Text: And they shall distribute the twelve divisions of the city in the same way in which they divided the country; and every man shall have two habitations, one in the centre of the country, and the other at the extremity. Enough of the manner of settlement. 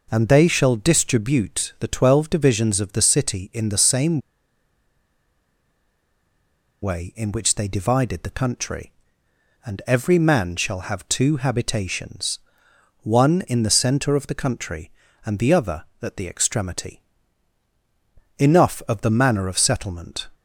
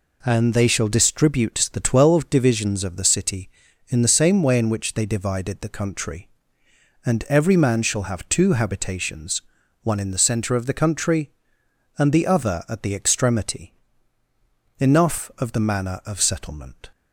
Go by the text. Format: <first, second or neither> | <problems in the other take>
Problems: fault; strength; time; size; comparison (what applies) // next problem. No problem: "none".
second | pauses between "same" and "way"; strong; at 4.1 s; 2.6 s long